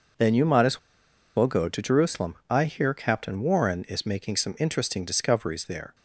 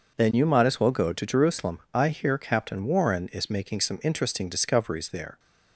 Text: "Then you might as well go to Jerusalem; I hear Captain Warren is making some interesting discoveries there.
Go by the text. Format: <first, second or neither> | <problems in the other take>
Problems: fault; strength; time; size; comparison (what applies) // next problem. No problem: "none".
second | pauses between "as" and "well"; noticeable; at 0.7 s; 0.57 s long